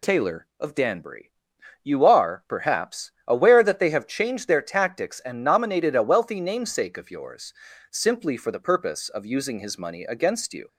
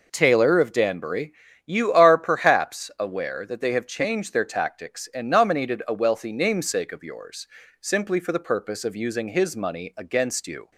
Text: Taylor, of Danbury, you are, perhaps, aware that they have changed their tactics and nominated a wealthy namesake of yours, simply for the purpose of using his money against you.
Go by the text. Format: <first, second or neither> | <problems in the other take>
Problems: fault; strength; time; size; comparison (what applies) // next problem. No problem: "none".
neither | none